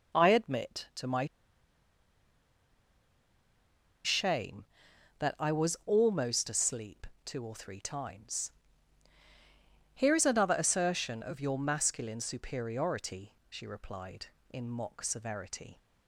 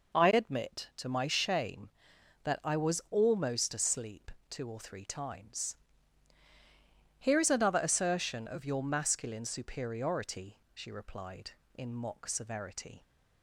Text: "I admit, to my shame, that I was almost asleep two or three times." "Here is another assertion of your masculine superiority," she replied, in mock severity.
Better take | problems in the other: second | pauses between "my" and "shame"; strong; at 1.2 s; 2.7 s long // pauses between "asleep" and "two"; slight; at 7.0 s; 0.18 s long; slight in the second

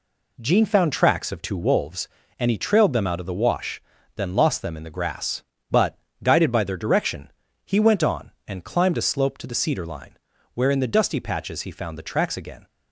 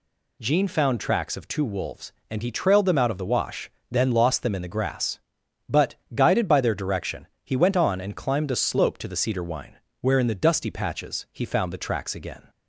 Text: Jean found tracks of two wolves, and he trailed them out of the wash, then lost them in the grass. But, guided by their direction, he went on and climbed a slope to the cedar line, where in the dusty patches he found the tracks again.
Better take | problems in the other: first | says "wine" for "line"; at 9.4 s

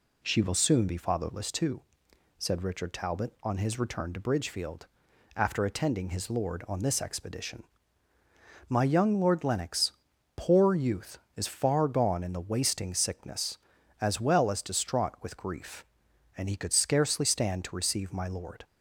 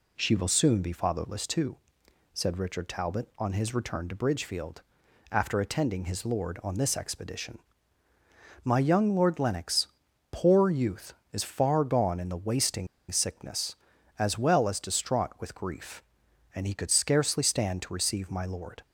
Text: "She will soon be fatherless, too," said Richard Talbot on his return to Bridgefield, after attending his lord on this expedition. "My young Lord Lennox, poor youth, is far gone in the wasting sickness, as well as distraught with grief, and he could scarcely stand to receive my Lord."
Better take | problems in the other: first | pauses between "wasting" and "sickness"; slight; at 12.8 s; 0.23 s long

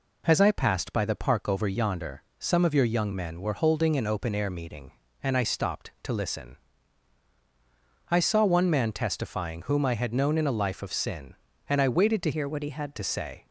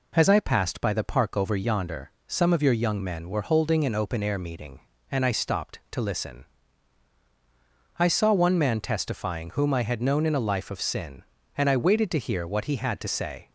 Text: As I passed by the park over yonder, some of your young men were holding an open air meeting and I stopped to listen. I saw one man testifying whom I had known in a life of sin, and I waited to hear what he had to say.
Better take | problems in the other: second | changes voice from "hear" to "had"; from 12.3 to 12.9 s; 0.6 s long

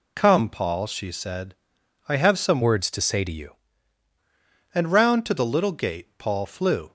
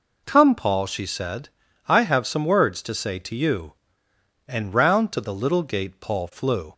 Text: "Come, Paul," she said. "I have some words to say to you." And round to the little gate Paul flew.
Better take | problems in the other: second | changes voice from "words" to "you"; from 2.6 to 3.5 s; 0.9 s long

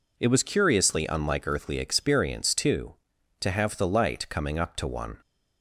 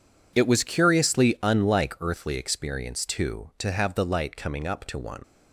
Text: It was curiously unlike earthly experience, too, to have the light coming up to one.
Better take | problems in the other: first | leaves "one" unfinished; at 5.2 s; 70 ms

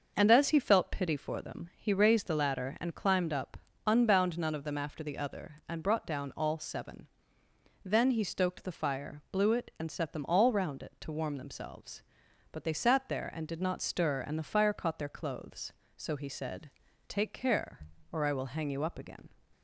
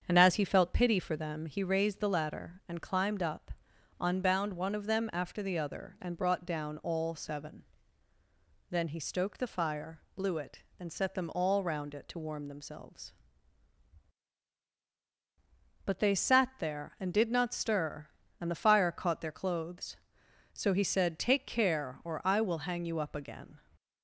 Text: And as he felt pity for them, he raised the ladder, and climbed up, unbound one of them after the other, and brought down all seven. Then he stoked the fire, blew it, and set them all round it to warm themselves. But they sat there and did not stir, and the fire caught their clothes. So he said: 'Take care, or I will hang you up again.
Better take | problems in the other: second | starts louder than the rest; noticeable; until 1.1 s; 6 dB; strong in the second // says "none" for "one"; at 4.3 s

